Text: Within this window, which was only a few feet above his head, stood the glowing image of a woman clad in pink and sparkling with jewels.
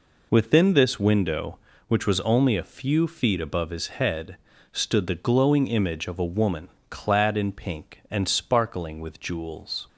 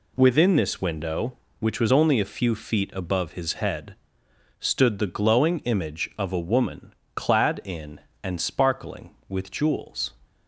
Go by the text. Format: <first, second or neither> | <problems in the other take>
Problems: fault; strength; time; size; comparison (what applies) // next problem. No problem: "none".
first | pauses between "woman" and "clad"; slight; at 6.9 s; 0.22 s long; slight in the first // skips "pink"; at 8.1 s